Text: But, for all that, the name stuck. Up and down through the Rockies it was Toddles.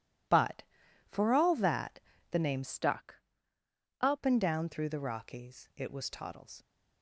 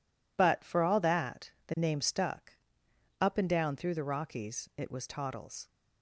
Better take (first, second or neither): second